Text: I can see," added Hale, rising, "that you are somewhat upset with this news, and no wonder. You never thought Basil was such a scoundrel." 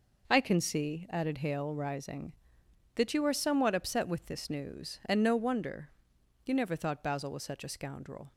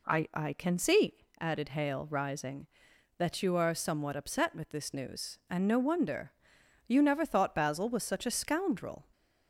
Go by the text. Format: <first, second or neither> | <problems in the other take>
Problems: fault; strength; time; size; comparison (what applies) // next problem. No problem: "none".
first | says "I" twice; at 0.3 s